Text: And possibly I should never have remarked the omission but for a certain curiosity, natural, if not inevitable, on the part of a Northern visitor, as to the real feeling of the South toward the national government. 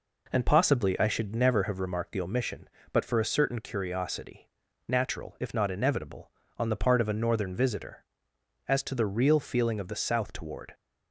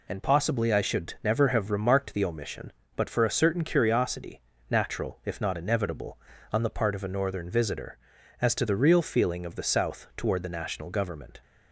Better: second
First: stops before "the national government"; at 10.7 s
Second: none

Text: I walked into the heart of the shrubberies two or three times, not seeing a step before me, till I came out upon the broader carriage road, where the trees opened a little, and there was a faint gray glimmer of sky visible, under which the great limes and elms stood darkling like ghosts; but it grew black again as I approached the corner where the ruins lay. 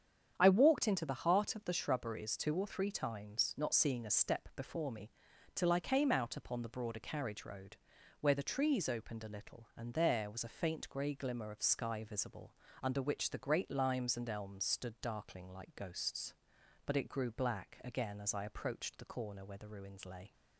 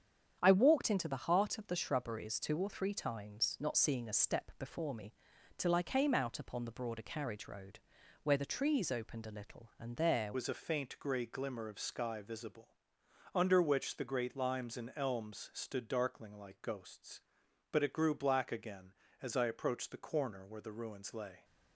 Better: first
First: starts louder than the rest; strong; until 1.3 s; 8 dB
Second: starts louder than the rest; strong; until 1.4 s; 8 dB // changes voice at "was"; from 10.3 s on; 11.1 s long

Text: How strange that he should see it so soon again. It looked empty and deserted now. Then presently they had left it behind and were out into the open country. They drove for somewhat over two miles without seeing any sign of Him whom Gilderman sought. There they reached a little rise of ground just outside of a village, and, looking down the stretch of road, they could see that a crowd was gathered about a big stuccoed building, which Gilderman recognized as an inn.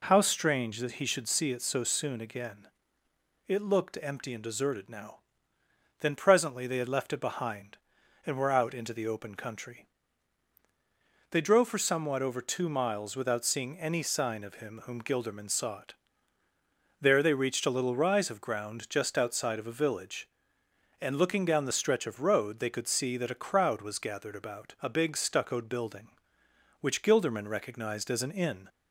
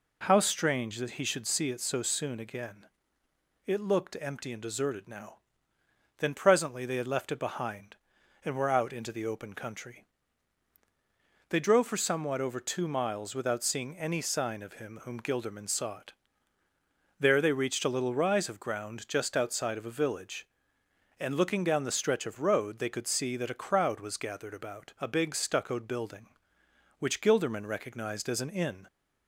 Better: neither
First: none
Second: none

